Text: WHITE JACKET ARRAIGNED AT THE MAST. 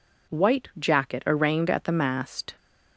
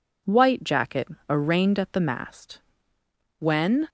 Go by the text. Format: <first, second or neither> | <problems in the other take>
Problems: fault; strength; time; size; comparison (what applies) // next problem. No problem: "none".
first | pauses between "JACKET" and "ARRAIGNED"; slight; at 1.0 s; 0.20 s long // goes on to say "When"; slight; from 3.4 s on; 0.48 s long